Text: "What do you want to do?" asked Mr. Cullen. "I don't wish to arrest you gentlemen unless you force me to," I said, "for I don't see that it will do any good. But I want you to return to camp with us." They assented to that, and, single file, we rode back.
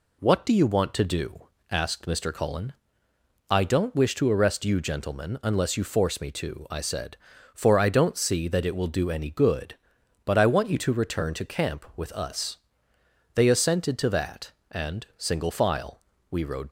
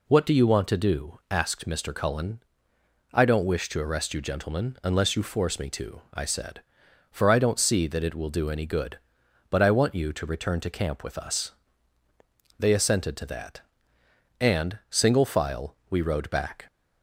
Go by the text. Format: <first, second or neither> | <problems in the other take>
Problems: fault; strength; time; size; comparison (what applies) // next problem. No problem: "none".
second | stops before "back"; at 16.6 s